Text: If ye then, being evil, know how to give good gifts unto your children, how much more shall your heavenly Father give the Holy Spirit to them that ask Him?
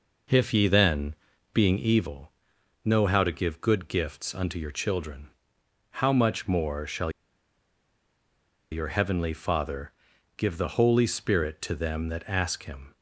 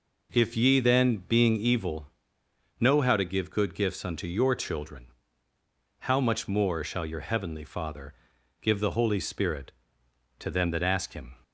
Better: second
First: pauses between "shall" and "your"; strong; at 7.1 s; 1.6 s long // pauses between "Father" and "give"; noticeable; at 9.9 s; 0.46 s long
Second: pauses between "Father" and "give"; noticeable; at 8.1 s; 0.48 s long

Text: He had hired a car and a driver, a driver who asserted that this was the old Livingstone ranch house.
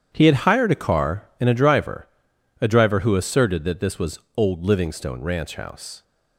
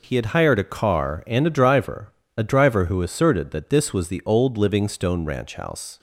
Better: second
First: starts louder than the rest; strong; until 1.1 s; 9 dB // skips "the"; at 4.2 s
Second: none

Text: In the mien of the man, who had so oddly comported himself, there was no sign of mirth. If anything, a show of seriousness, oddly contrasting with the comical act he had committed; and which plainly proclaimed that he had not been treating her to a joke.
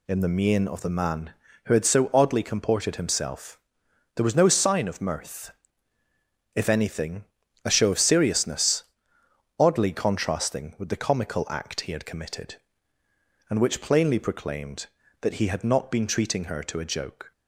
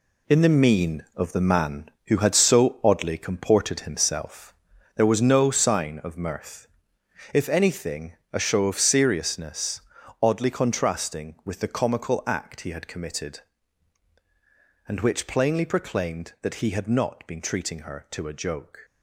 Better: first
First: none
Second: gets quieter; strong; throughout; 8.5 dB

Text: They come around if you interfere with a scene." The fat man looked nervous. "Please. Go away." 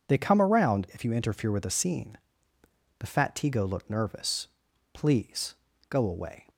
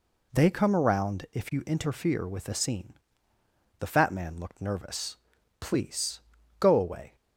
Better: second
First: says "tigo" for "man"; at 3.3 s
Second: none

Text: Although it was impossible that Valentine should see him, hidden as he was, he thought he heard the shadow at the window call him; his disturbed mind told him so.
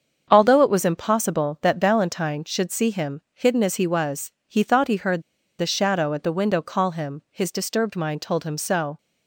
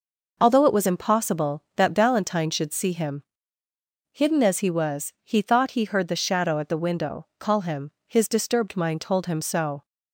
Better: second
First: starts louder than the rest; strong; until 1.3 s; 7 dB // pauses between "heard" and "the"; at 5.2 s; 0.37 s long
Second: none

